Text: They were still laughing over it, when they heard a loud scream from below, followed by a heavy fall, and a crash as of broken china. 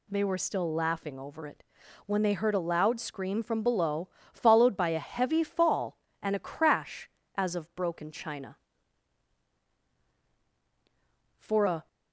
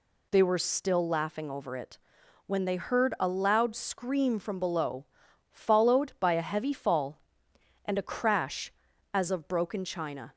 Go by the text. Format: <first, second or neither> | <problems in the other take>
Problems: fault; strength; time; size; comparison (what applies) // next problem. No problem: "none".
second | goes on to say "For a"; from 11.3 s on; 0.48 s long